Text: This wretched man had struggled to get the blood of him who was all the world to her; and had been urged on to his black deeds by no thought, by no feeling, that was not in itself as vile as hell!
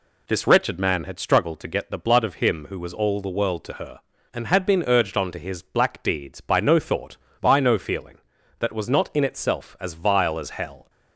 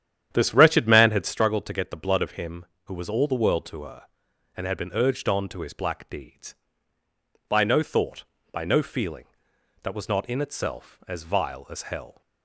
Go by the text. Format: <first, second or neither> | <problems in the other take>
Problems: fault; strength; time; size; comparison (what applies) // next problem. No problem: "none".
first | starts louder than the rest; strong; until 1.4 s; 10 dB